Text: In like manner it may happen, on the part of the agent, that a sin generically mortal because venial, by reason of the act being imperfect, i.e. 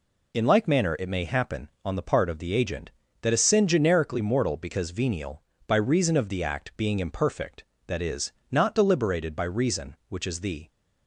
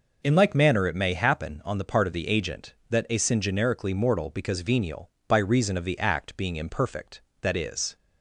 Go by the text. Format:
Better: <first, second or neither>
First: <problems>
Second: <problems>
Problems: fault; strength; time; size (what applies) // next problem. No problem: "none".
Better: second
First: goes on to say "not deliberated by reason which is the"; strong; from 8.5 s on; 2.1 s long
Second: none